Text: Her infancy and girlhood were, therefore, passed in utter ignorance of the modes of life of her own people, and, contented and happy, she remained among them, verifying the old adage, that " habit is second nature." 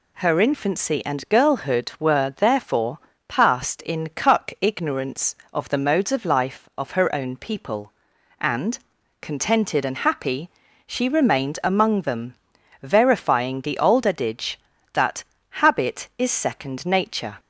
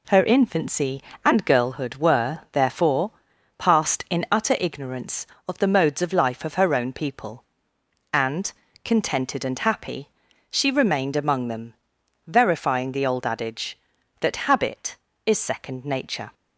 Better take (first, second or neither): second